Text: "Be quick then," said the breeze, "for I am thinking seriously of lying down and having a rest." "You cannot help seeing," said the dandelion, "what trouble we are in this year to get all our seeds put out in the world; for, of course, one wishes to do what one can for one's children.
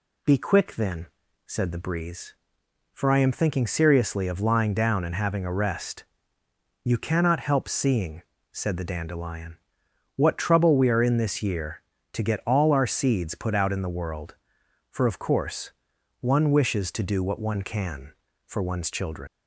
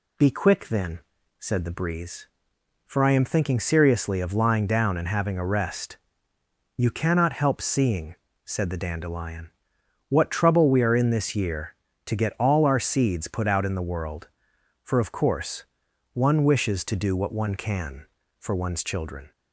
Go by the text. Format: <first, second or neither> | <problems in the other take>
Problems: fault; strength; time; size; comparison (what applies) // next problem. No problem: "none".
second | leaves "children" unfinished; at 19.2 s; 110 ms